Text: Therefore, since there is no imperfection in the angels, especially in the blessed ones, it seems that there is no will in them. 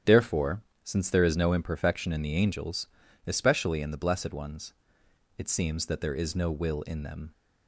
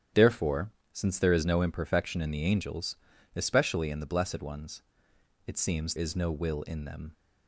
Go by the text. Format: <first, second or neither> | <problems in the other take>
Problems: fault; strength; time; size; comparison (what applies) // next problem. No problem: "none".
first | starts louder than the rest; strong; until 1.3 s; 9.5 dB; strong in the first // skips "that there"; at 5.9 s